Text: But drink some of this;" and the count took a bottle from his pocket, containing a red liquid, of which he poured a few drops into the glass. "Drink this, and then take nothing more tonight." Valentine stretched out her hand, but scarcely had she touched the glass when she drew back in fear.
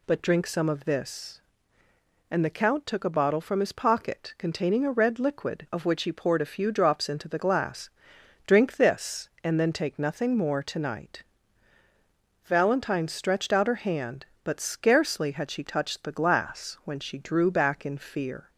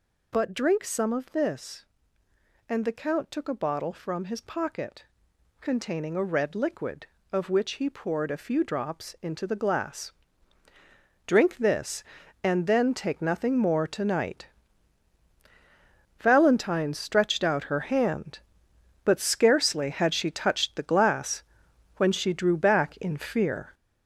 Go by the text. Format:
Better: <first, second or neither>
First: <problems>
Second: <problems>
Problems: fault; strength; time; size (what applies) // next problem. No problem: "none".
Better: first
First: none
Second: gets louder; throughout; 6.5 dB // pauses between "glass" and "when"; noticeable; at 21.4 s; 0.54 s long